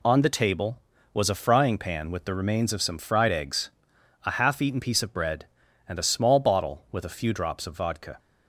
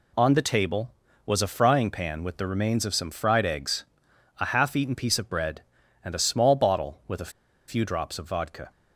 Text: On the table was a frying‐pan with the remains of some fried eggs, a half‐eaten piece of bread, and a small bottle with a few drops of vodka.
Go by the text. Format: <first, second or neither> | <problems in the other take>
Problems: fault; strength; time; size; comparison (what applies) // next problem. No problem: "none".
first | pauses between "a" and "few"; at 7.3 s; 0.37 s long